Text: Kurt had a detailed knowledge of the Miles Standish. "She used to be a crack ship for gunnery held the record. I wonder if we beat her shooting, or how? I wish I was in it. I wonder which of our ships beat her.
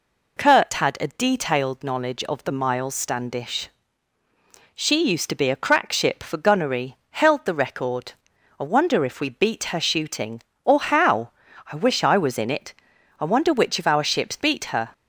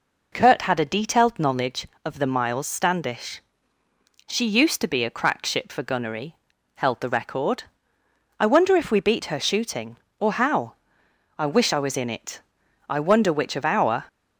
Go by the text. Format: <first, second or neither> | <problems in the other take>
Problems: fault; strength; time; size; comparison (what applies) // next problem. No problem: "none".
first | pauses between "gunnery" and "held"; at 6.3 s; 0.44 s long // stops before "ships beat her"; at 14.0 s